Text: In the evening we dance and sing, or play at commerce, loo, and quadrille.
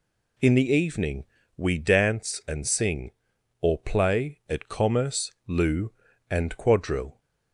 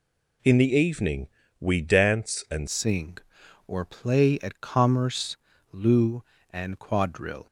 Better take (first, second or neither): first